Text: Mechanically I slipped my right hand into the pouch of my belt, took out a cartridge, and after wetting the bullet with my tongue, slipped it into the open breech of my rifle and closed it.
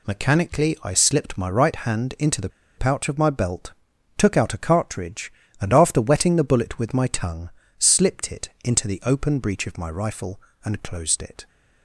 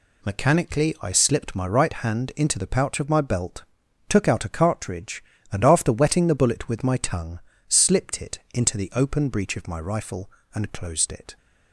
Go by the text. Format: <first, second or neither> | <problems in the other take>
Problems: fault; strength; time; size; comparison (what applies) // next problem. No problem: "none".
second | pauses between "the" and "pouch"; slight; at 2.4 s; 0.29 s long